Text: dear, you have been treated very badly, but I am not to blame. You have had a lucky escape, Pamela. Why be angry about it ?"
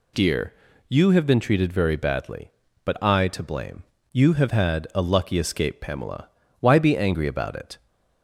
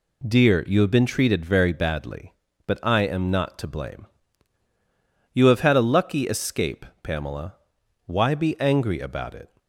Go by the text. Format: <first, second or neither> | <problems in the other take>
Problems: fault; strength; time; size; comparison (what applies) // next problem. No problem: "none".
second | skips "am not"; at 3.2 s